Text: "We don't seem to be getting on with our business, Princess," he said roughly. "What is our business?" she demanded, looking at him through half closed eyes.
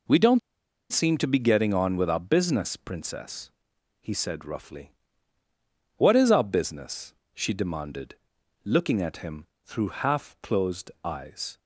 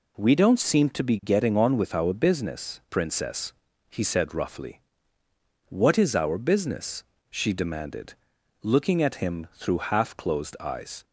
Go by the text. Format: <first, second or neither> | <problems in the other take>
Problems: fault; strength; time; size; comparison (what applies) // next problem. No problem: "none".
second | pauses between "don't" and "seem"; noticeable; at 0.3 s; 0.52 s long // pauses between "him" and "through"; slight; at 9.4 s; 0.20 s long